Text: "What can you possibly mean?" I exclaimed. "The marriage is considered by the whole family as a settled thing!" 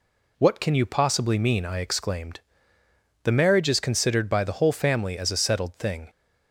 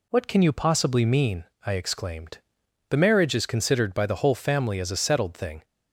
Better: neither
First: none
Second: none

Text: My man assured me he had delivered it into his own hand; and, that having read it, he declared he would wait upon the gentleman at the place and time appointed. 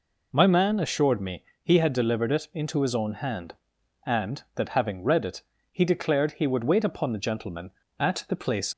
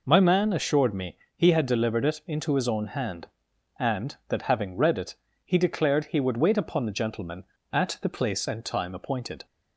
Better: second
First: pauses between "me" and "he"; slight; at 1.4 s; 0.22 s long // stops before "and time appointed"; at 8.7 s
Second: pauses between "me" and "he"; slight; at 1.1 s; 0.22 s long

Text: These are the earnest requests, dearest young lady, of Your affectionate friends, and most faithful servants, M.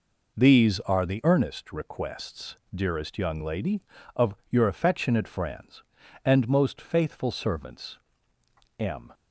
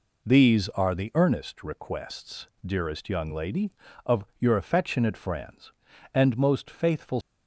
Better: first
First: none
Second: stops before "servants M"; at 7.2 s

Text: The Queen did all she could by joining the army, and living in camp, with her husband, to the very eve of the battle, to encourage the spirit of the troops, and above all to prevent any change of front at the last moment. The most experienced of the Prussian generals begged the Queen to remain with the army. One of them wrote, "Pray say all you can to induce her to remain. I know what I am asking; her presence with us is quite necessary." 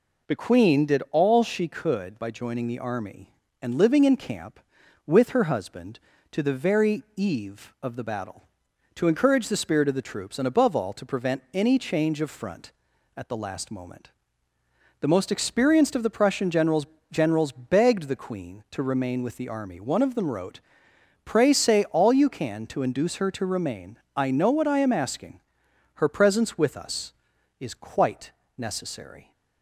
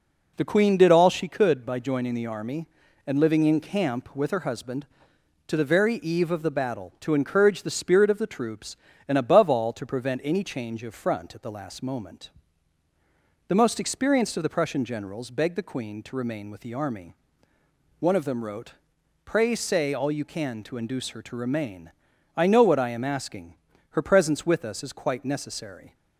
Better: second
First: says "generals" twice; at 17.1 s // pauses between "quite" and "necessary"; slight; at 28.3 s; 0.26 s long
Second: none

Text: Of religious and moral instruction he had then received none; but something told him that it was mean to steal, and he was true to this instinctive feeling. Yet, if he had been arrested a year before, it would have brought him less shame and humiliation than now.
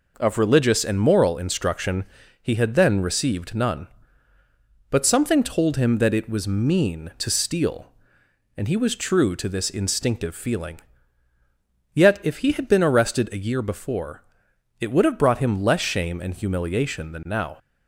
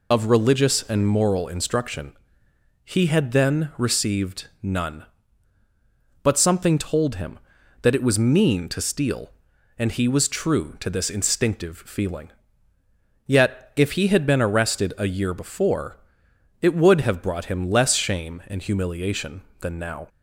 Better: first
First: pauses between "instruction" and "he"; slight; at 2.0 s; 0.36 s long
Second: loses the start of "Of"; at 0.1 s; 55 ms // pauses between "instruction" and "he"; noticeable; at 2.1 s; 0.68 s long // pauses between "received" and "none"; slight; at 4.4 s; 0.16 s long

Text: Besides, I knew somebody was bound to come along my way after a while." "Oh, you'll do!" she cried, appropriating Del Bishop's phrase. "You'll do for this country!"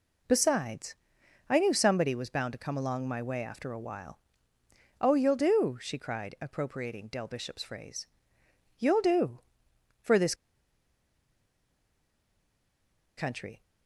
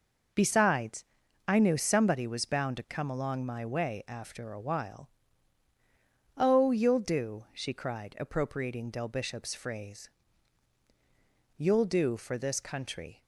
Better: second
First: pauses between "this" and "country"; strong; at 10.3 s; 2.8 s long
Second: none

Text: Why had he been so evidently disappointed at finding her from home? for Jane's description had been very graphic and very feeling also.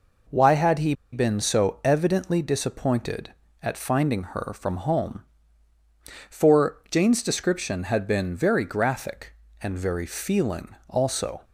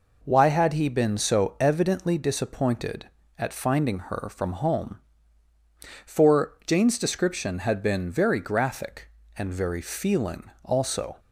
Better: second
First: pauses between "he" and "been"; slight; at 0.9 s; 0.19 s long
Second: none

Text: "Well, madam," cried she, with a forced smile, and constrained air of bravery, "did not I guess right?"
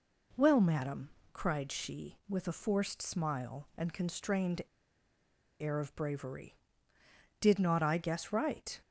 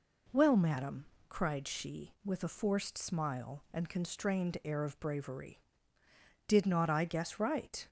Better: second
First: pauses between "constrained" and "air"; at 4.6 s; 0.99 s long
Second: none

